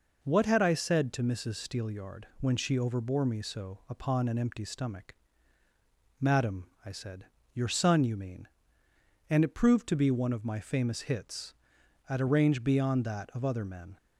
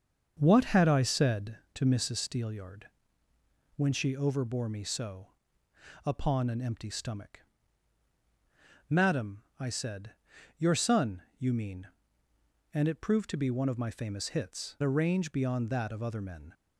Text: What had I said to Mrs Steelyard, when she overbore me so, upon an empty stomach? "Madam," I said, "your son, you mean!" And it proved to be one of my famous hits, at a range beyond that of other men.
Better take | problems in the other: first | starts louder than the rest; until 1.4 s; 6.5 dB // skips "at"; at 14.7 s

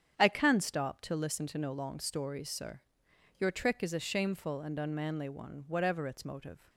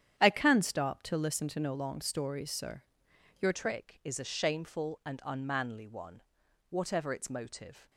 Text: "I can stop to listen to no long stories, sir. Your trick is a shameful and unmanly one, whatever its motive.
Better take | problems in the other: first | starts louder than the rest; strong; until 1.1 s; 9.5 dB; strong in the first // changes voice at "trick"; from 3.5 s on; 4.3 s long

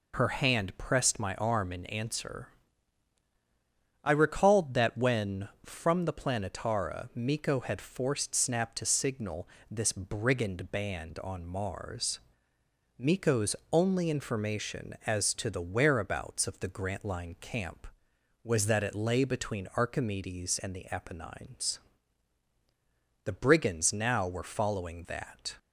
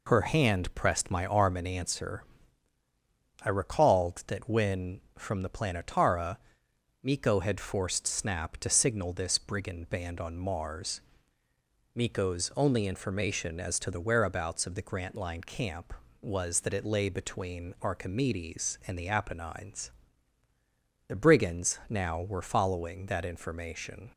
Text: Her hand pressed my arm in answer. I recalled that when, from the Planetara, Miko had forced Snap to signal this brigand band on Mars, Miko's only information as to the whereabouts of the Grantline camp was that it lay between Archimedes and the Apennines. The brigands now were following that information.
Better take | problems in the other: second | pauses between "signal" and "this"; slight; at 9.4 s; 0.20 s long // pauses between "Miko's" and "only"; slight; at 13.5 s; 0.16 s long // stops before "information"; at 25.5 s

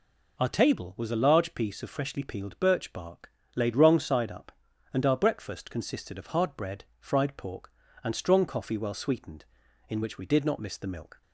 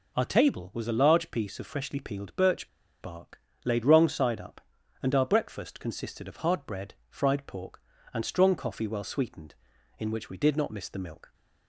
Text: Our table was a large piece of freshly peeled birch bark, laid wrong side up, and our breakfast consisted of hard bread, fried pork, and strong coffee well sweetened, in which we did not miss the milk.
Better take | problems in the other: first | pauses between "birch" and "bark"; slight; at 2.6 s; 0.32 s long

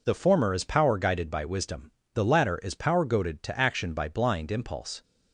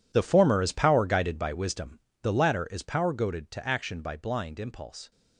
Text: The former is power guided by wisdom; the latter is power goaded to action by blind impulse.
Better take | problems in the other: first | gets quieter; strong; throughout; 16 dB

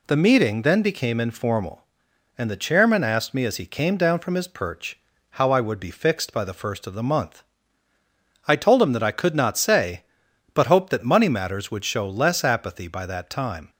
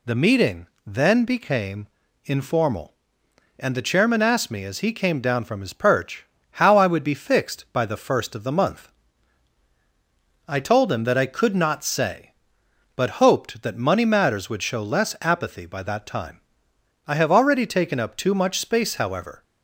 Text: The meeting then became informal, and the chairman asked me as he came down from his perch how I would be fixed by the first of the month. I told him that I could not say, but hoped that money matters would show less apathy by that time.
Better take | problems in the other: first | pauses between "meeting" and "then"; slight; at 0.6 s; 0.18 s long // pauses between "became" and "informal"; at 1.8 s; 0.38 s long // pauses between "perch" and "how"; slight; at 6.2 s; 0.32 s long; slight in the first // goes on to say "I have already taken up too much space however"; strong; from 17.0 s on; 2.3 s long

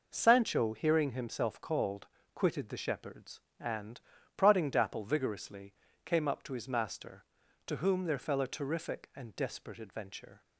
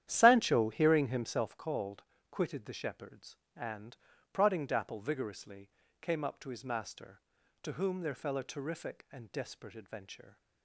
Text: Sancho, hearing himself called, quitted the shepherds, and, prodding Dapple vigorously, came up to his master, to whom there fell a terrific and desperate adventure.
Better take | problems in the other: first | starts louder than the rest; strong; until 1.6 s; 11 dB

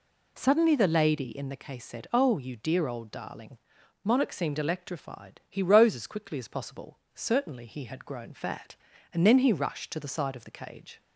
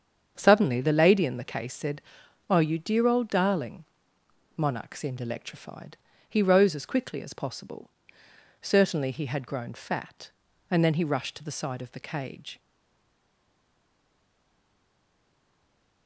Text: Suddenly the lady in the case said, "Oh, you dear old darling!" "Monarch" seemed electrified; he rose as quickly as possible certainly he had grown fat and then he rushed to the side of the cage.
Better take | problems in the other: first | starts louder than the rest; strong; until 1.3 s; 7.5 dB // pauses between "possible" and "certainly"; noticeable; at 7.8 s; 0.74 s long; slight in the first // stays silent after the last word; strong; from 12.5 s on; 3.5 s long

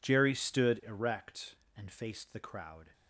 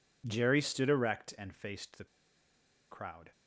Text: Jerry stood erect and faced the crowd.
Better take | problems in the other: first | pauses between "the" and "crowd"; noticeable; at 2.0 s; 0.86 s long

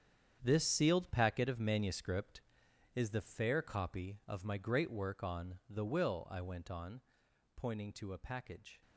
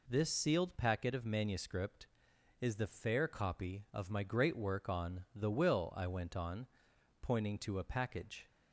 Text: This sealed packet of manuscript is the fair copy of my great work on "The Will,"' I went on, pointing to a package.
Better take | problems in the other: second | gets quieter; strong; throughout; 12 dB

